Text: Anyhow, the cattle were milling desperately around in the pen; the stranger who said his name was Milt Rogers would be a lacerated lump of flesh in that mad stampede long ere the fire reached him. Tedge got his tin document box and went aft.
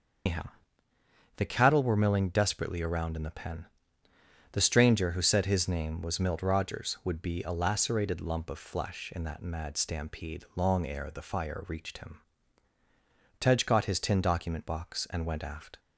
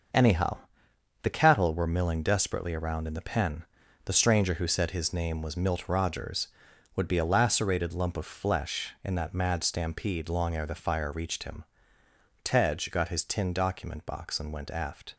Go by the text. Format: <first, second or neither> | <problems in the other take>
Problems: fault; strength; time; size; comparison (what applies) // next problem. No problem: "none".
second | loses the start of "Anyhow"; at 0.2 s; 140 ms // starts louder than the rest; until 2.1 s; 6.5 dB; also in the second